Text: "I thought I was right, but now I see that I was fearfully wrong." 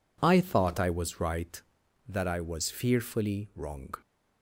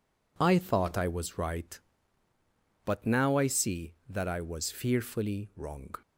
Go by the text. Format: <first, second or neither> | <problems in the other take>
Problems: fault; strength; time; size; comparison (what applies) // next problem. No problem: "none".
second | skips "but now I see"; at 1.8 s